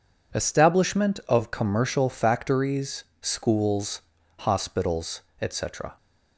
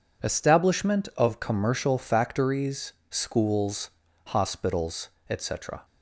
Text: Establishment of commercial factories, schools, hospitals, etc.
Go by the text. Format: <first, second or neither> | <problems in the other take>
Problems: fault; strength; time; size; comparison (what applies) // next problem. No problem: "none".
neither | none